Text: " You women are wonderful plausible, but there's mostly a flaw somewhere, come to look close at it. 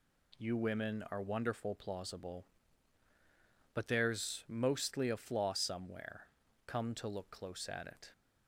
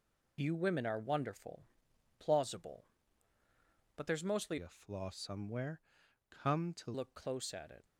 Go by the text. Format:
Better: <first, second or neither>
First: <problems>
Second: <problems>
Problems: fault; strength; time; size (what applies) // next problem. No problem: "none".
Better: first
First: none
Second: pauses between "wonderful" and "plausible"; noticeable; at 1.6 s; 0.52 s long // changes voice from "a" to "to"; from 4.5 to 6.9 s; 2.4 s long